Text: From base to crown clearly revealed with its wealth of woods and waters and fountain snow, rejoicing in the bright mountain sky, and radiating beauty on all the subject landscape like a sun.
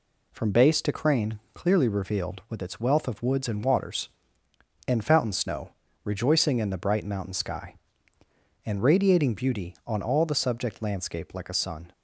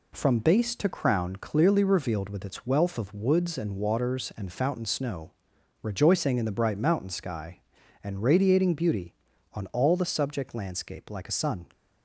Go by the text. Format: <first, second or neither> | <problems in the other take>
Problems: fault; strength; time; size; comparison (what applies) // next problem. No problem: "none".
second | says "crane" for "crown"; at 0.9 s